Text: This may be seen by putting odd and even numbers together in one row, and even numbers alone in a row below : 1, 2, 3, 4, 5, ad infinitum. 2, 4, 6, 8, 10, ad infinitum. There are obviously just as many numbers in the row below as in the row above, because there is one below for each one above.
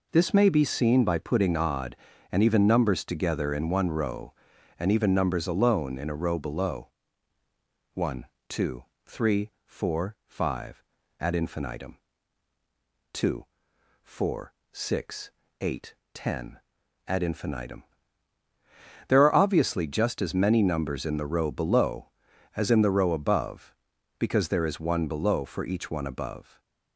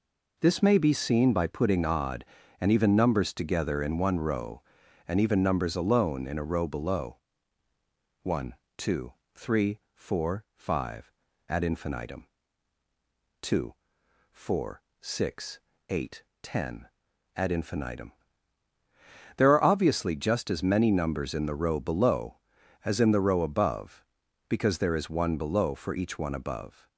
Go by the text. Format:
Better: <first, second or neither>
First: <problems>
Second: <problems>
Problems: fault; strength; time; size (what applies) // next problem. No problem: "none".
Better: neither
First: none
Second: none